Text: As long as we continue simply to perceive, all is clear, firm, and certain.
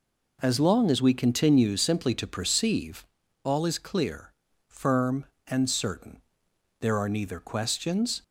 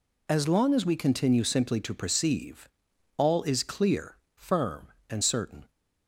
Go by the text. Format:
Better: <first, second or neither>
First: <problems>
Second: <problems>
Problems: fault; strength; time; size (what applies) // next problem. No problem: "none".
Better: second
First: goes on to say "There are neither questions"; from 6.7 s on; 1.4 s long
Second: none